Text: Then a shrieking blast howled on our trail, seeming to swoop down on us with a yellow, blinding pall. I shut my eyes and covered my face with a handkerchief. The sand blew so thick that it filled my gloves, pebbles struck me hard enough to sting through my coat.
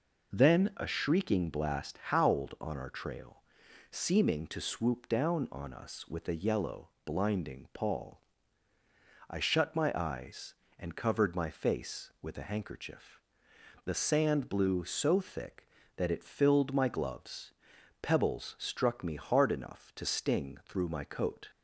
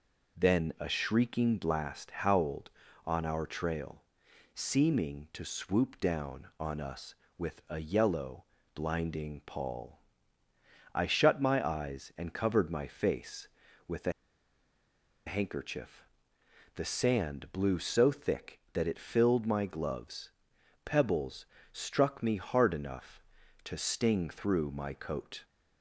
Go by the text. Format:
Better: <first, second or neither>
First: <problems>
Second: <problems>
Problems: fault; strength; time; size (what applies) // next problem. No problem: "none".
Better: first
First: none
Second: pauses between "a" and "handkerchief"; at 14.1 s; 1.1 s long // pauses between "pebbles" and "struck"; slight; at 21.4 s; 0.26 s long